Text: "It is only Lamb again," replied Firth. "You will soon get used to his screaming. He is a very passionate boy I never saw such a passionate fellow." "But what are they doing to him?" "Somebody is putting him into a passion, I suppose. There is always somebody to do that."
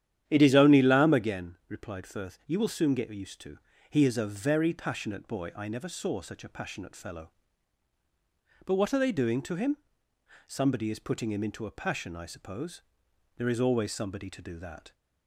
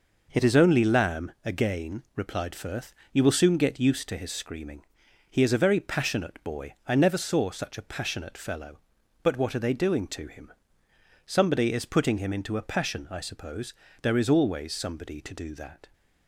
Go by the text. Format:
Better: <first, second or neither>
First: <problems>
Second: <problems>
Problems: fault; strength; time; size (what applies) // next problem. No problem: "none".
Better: second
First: starts louder than the rest; strong; until 1.2 s; 10.5 dB // skips "his screaming"; at 3.7 s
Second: none